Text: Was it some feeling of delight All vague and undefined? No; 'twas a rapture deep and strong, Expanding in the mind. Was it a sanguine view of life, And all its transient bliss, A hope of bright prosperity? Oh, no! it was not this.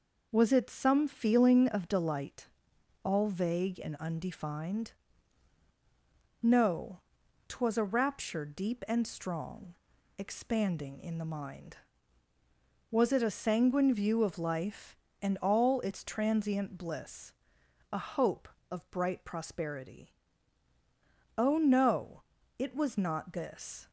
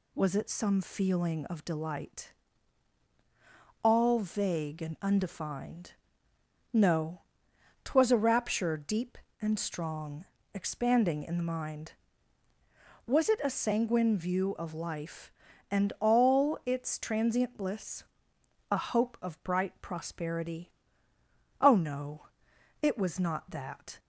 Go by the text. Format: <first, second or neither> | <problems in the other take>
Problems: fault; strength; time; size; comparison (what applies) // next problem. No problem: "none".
first | pauses between "delight" and "All"; strong; at 2.3 s; 1.5 s long; noticeable in the first // says "that" for "this"; at 23.4 s